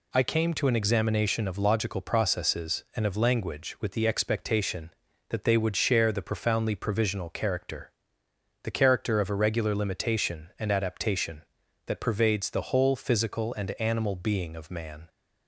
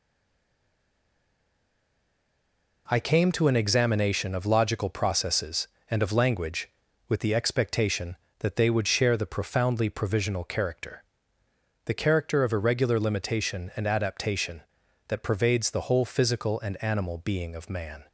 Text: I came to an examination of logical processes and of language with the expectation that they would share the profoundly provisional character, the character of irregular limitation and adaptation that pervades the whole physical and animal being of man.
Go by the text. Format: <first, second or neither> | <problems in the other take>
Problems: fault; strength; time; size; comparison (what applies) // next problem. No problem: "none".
first | stays silent before the first word; strong; until 2.8 s; 2.8 s long